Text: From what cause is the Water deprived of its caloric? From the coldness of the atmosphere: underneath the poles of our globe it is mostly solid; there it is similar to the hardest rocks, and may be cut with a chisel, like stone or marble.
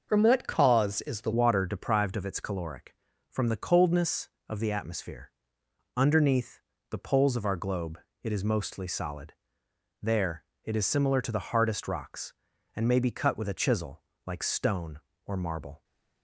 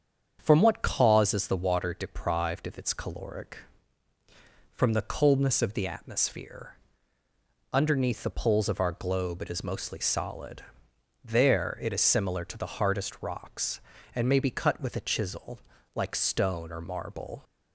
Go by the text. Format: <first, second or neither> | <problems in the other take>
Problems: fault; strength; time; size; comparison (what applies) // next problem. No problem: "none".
second | starts louder than the rest; noticeable; until 1.0 s; 6 dB; strong in the second // changes voice at "Water"; from 1.3 s on; 14.5 s long // pauses between "underneath" and "the"; slight; at 6.6 s; 0.28 s long // pauses between "globe" and "it"; slight; at 7.9 s; 0.24 s long // pauses between "there" and "it"; slight; at 10.4 s; 0.18 s long